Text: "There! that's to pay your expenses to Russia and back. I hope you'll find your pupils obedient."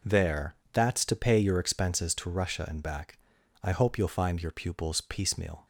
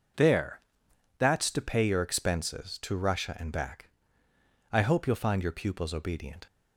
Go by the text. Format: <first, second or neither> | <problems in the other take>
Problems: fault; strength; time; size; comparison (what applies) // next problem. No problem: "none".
second | says "piecemeal" for "obedient"; at 4.9 s